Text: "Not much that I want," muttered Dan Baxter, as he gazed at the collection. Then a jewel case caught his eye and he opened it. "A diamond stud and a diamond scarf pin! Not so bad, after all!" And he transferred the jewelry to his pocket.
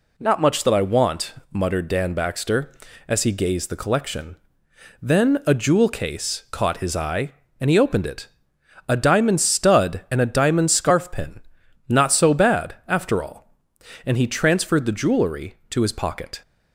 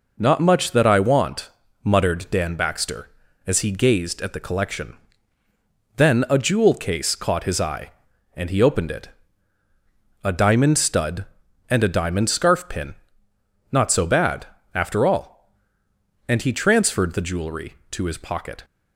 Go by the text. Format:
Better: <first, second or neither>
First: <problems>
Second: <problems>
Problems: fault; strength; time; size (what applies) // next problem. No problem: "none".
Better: second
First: skips "at"; at 3.6 s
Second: none